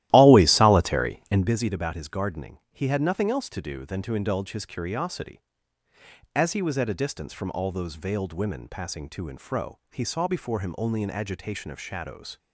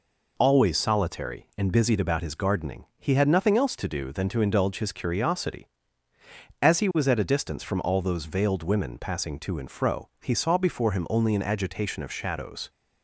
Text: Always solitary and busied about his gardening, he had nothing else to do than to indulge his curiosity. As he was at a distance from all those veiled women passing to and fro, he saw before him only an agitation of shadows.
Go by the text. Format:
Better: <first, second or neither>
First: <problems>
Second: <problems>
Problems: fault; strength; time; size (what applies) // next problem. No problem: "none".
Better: second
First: starts louder than the rest; strong; until 1.5 s; 14.5 dB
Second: none